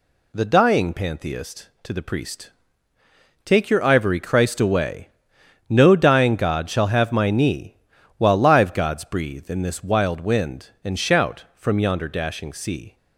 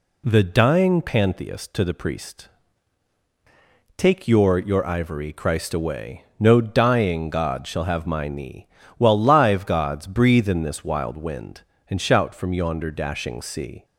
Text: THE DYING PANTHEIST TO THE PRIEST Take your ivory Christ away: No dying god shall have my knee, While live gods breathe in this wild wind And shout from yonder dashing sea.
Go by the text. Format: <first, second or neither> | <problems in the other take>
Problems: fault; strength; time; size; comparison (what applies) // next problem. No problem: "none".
first | pauses between "PRIEST" and "Take"; strong; at 2.4 s; 1.5 s long; noticeable in the first // says "your" twice; at 4.5 s